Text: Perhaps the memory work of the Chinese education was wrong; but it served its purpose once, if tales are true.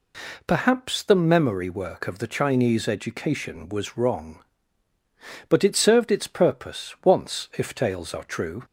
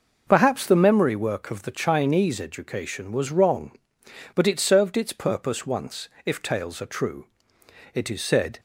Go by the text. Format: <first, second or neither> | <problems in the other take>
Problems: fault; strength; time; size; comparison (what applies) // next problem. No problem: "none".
first | goes on to say "It is said"; noticeable; from 7.9 s on; 0.66 s long